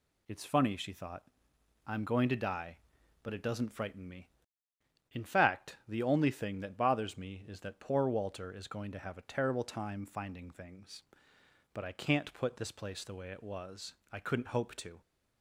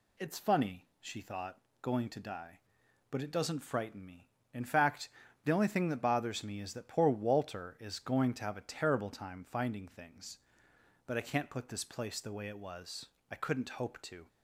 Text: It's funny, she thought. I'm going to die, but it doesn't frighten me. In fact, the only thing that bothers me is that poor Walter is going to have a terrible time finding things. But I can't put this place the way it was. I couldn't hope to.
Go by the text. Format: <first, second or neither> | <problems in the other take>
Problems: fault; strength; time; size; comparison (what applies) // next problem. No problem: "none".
first | skips "I'm"; at 1.7 s